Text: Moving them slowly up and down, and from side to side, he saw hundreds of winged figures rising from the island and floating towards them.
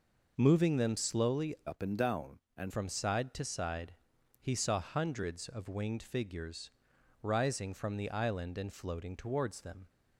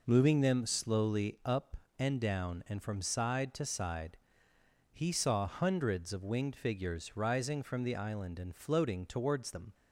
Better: second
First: changes voice from "up" to "and"; from 1.6 to 2.7 s; 1.1 s long // pauses between "figures" and "rising"; noticeable; at 6.6 s; 0.54 s long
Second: none

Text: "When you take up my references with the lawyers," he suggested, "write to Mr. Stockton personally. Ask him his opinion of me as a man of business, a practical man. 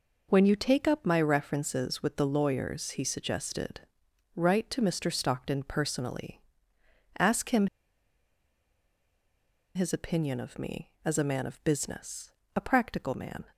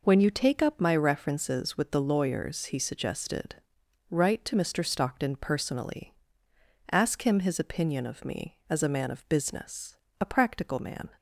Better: second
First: pauses between "him" and "his"; strong; at 7.6 s; 2.0 s long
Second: none

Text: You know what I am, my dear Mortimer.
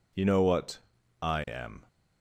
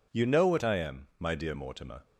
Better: second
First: pauses between "what" and "I"; at 0.7 s; 0.42 s long // stops before "my dear Mortimer"; at 1.8 s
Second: none

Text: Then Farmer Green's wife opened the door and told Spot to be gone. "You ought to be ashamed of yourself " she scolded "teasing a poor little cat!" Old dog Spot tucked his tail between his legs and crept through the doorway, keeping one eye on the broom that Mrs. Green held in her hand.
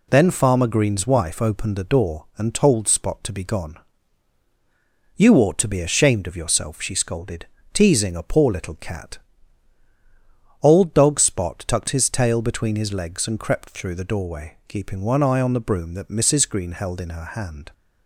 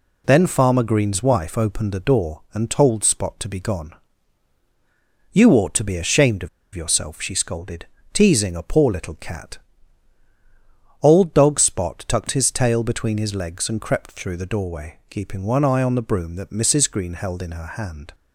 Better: first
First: pauses between "scolded" and "teasing"; slight; at 7.4 s; 0.28 s long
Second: pauses between "of" and "yourself"; slight; at 6.4 s; 0.26 s long // pauses between "scolded" and "teasing"; slight; at 7.8 s; 0.28 s long

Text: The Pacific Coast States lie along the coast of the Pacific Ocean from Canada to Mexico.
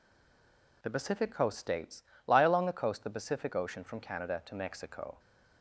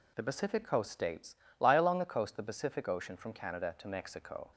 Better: second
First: stays silent before the first word; slight; until 0.8 s; 0.8 s long // pauses between "States" and "lie"; slight; at 2.0 s; 0.24 s long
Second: pauses between "States" and "lie"; slight; at 1.3 s; 0.24 s long

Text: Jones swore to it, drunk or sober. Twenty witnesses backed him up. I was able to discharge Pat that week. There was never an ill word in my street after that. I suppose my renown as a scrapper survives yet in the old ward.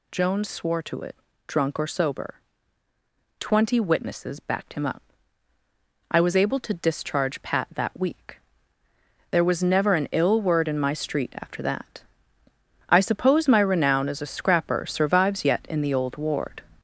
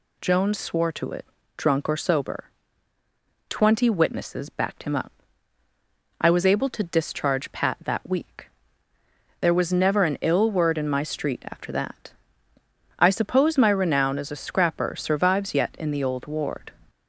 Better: second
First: gets louder; noticeable; throughout; 5 dB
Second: none

